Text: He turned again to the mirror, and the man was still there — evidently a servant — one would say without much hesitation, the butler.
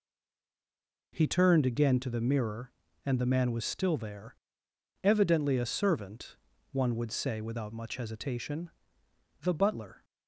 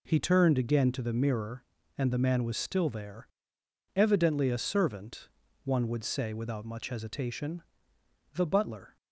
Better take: second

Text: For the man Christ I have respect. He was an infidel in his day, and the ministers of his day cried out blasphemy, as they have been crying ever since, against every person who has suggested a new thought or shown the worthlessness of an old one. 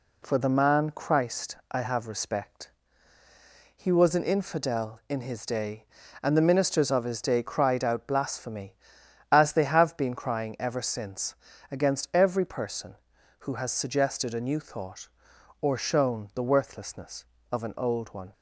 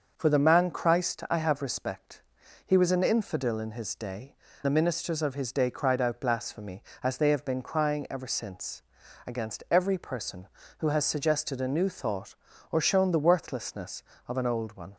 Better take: first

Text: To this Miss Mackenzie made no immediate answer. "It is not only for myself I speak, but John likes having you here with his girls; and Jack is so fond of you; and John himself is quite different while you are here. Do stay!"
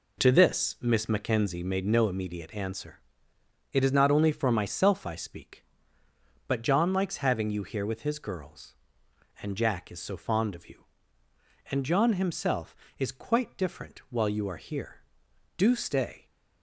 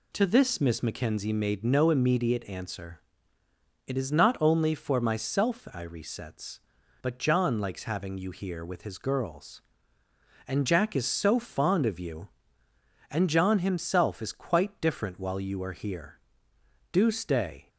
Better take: first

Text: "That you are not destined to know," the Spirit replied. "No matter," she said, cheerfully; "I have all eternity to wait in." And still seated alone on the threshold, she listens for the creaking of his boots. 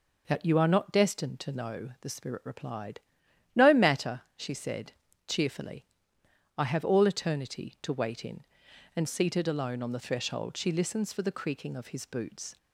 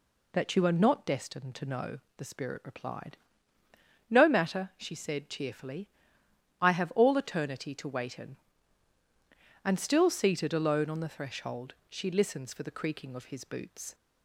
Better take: second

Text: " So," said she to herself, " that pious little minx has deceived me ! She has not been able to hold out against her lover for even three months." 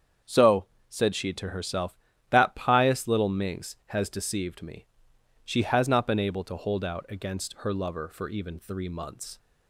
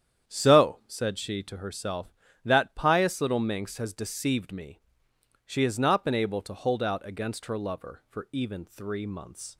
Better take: neither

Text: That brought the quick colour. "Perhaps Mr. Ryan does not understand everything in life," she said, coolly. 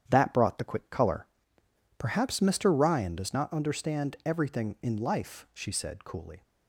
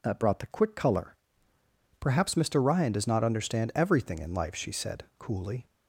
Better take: second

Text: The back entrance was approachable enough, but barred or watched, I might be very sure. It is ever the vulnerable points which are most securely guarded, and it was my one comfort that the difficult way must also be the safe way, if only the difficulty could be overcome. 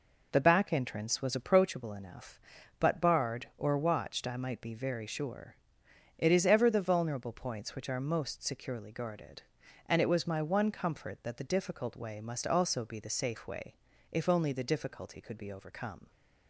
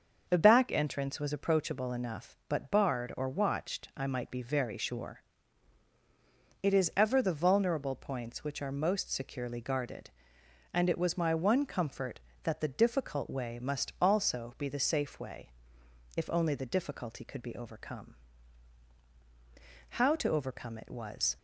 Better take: first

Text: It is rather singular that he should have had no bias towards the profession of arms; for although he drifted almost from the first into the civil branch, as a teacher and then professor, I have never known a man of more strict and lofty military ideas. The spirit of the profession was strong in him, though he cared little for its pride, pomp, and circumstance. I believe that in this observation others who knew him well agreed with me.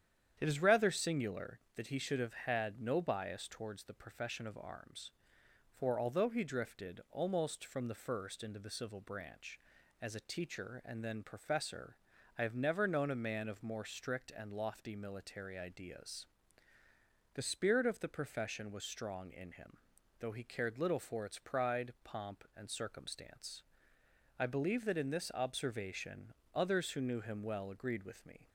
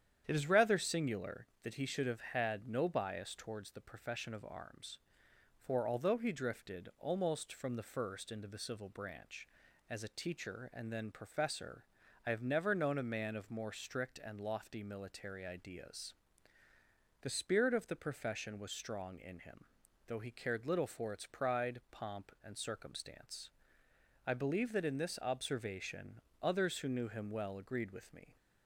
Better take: neither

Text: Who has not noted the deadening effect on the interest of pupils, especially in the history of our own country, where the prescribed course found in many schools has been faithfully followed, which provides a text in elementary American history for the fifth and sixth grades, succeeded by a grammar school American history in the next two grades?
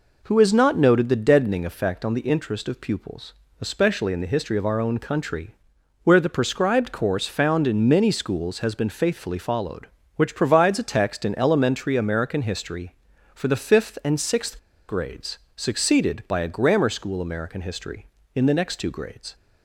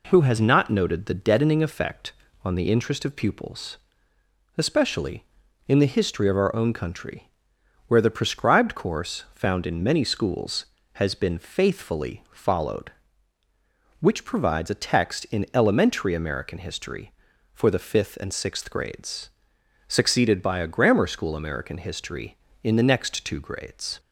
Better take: second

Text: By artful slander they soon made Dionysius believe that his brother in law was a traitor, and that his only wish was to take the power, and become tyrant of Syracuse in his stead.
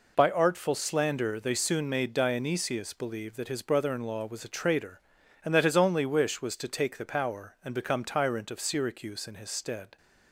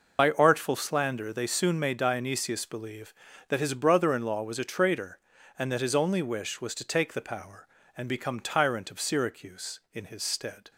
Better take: first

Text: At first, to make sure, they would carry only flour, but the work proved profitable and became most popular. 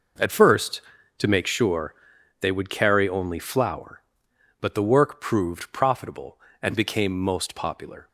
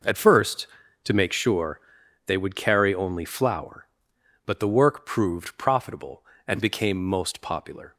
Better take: neither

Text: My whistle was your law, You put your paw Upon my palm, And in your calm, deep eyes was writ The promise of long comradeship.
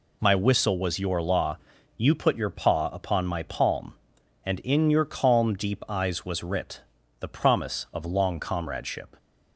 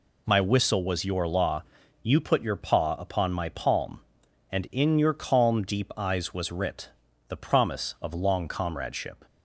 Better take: neither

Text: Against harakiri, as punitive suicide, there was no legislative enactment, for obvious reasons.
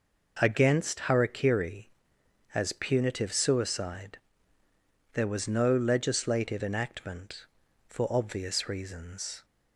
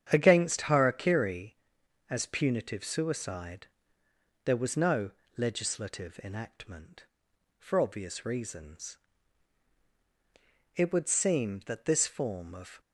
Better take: first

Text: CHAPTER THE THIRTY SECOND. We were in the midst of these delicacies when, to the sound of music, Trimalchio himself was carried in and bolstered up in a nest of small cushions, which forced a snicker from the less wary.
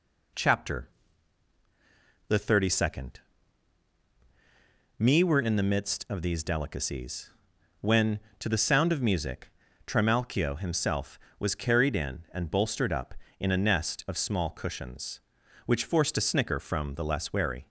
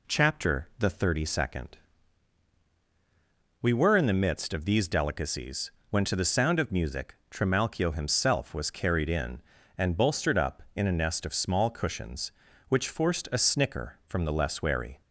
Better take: second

